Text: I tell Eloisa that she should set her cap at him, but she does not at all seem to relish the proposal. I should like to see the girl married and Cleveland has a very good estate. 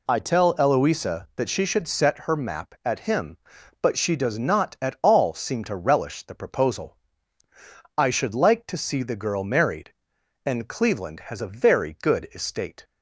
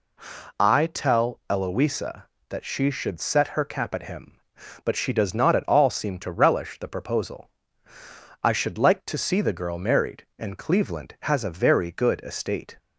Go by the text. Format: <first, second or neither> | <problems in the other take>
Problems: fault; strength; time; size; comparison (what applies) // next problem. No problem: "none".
second | says "map" for "cap"; at 2.3 s